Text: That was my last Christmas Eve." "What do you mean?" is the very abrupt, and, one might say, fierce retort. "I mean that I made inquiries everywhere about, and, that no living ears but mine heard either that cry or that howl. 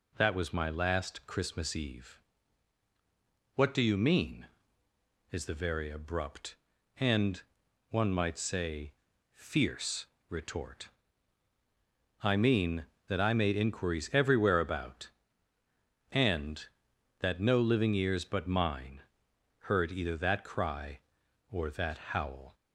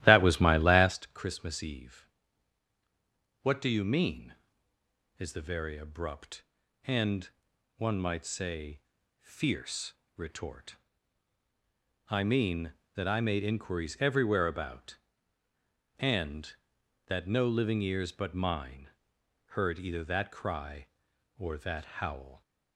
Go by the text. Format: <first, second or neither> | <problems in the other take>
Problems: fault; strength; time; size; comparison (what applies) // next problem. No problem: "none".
first | starts louder than the rest; strong; until 1.0 s; 14 dB // pauses between "fierce" and "retort"; slight; at 9.9 s; 0.24 s long; slight in the first // pauses between "mine" and "heard"; noticeable; at 18.8 s; 0.60 s long; noticeable in the first // pauses between "that" and "howl"; slight; at 21.8 s; 0.16 s long; slight in the first